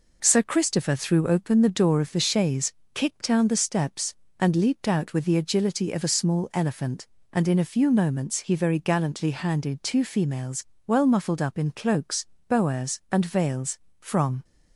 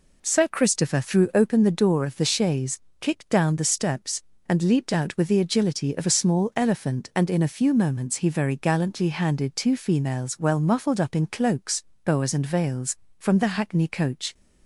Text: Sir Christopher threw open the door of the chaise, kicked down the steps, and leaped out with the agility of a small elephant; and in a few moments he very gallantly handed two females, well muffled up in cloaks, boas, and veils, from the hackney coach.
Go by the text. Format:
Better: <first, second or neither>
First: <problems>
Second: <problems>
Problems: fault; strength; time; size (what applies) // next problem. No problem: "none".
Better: second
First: stops before "the hackney coach"; at 14.4 s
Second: none